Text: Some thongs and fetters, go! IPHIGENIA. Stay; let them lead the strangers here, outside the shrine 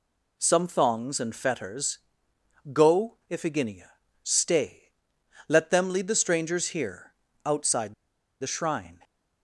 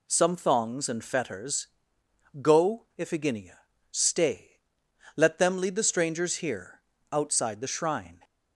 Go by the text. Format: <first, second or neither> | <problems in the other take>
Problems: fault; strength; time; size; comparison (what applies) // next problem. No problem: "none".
second | pauses between "outside" and "the"; noticeable; at 7.9 s; 0.47 s long